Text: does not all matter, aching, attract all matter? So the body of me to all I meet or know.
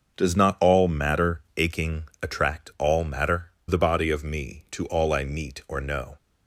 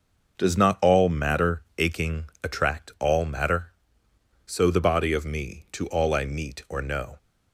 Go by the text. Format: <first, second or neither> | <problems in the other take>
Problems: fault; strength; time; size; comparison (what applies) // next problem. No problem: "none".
second | starts louder than the rest; until 1.2 s; 6.5 dB // skips "So"; at 3.5 s